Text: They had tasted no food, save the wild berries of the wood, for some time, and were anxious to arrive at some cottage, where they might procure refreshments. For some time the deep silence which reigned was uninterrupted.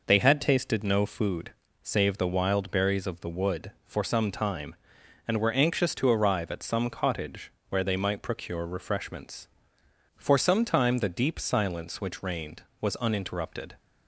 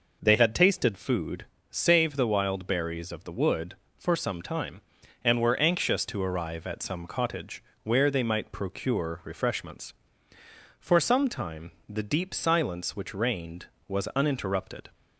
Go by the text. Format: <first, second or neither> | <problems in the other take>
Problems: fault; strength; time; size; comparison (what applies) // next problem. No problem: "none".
first | skips "no"; at 0.9 s // pauses between "time" and "the"; slight; at 11.7 s; 0.16 s long